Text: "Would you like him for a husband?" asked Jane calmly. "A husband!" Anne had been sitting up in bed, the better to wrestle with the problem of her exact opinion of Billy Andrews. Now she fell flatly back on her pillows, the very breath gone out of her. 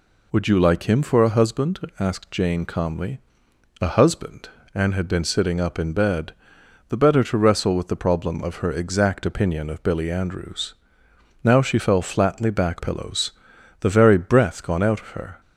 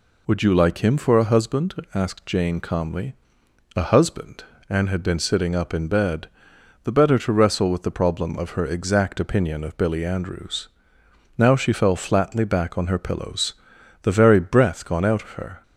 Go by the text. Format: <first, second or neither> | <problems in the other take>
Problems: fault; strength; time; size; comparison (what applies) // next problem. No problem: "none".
second | skips "on her"; at 12.7 s